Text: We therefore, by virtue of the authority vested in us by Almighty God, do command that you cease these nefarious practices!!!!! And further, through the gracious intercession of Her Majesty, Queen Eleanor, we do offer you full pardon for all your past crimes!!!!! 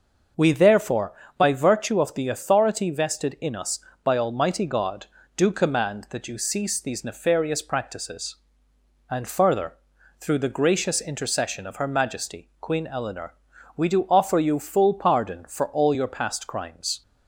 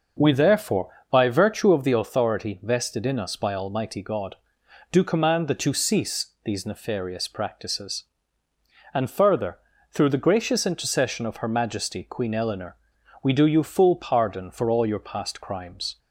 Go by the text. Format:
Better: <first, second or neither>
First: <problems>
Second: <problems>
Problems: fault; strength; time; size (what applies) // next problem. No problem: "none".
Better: first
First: none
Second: skips "offer"; at 13.4 s